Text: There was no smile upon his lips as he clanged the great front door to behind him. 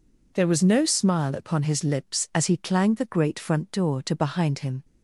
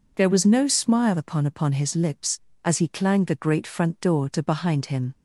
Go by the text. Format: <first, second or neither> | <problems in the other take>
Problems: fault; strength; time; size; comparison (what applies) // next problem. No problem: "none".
first | says "upon" twice; at 1.4 s